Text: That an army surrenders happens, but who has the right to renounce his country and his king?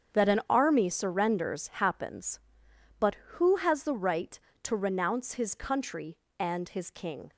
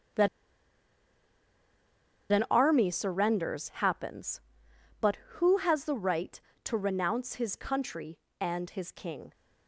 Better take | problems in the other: first | starts louder than the rest; strong; until 3.2 s; 7.5 dB; strong in the first // pauses between "That" and "an"; strong; at 0.2 s; 2.0 s long

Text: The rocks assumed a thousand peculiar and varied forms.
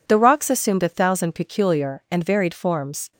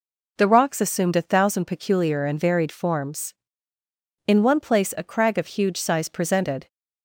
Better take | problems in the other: first | goes on to say "In one place a crag of huge size presented"; strong; from 4.2 s on; 2.4 s long

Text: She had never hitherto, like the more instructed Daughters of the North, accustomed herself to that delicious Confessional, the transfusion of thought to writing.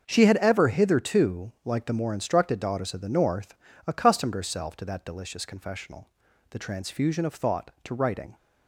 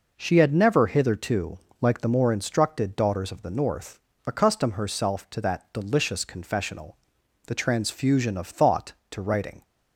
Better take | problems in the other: second | starts louder than the rest; until 1.0 s; 6.5 dB // says "ever" for "never"; at 0.3 s

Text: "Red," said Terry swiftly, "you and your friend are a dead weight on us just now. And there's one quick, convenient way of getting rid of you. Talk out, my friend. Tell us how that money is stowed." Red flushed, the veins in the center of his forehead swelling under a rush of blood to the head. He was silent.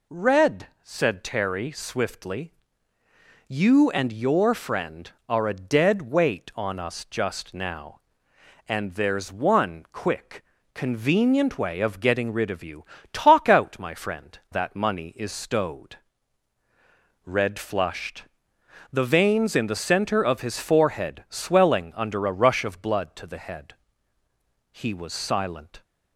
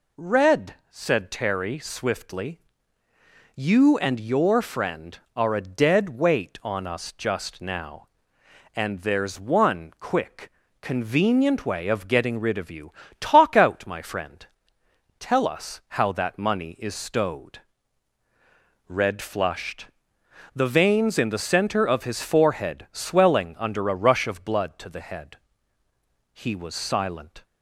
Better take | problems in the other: second | skips "Tell us how"; at 14.4 s

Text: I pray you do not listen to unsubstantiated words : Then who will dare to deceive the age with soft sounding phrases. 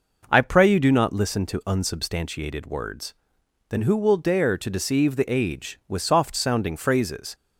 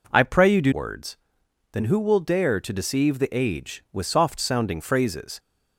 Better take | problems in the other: first | skips "not listen to unsubstantiated"; at 0.7 s

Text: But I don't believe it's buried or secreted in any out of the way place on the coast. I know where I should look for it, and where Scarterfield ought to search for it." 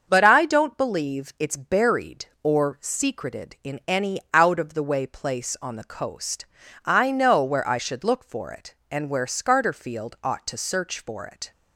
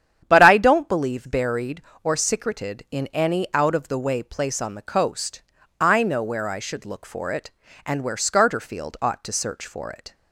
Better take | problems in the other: first | starts louder than the rest; strong; until 1.2 s; 9.5 dB; also in the first // skips "it's"; at 1.2 s

